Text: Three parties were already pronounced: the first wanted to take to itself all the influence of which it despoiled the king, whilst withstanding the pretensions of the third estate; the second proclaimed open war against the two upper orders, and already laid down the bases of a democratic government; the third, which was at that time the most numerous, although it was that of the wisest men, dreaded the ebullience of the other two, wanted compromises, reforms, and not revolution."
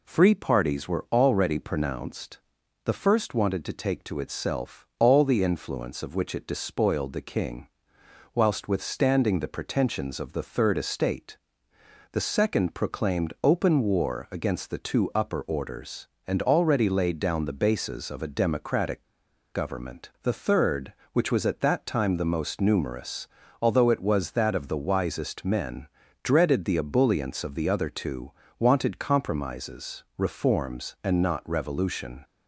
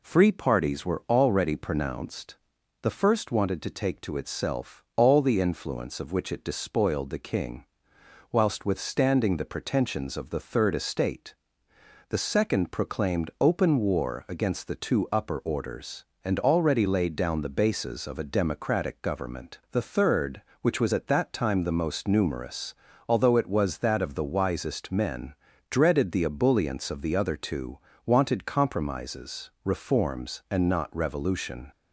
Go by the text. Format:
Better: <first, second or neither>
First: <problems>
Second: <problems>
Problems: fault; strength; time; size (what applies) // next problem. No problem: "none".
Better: second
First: pauses between "democratic" and "government"; noticeable; at 19.0 s; 0.48 s long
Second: none